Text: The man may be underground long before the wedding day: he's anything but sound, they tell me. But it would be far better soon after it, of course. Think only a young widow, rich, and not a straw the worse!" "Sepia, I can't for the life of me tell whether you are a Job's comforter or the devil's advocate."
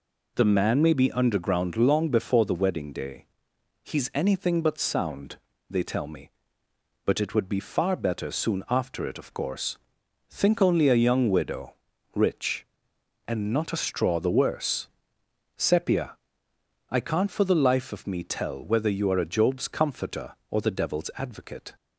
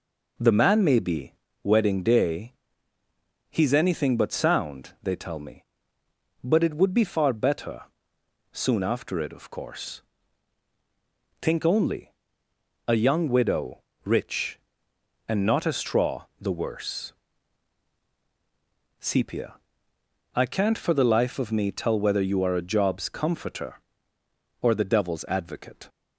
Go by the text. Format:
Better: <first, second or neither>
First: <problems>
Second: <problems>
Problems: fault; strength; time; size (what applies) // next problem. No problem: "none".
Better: first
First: none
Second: skips "underground long before the"; at 1.4 s // pauses between "better" and "soon"; noticeable; at 7.8 s; 0.72 s long // pauses between "only" and "a"; noticeable; at 12.1 s; 0.74 s long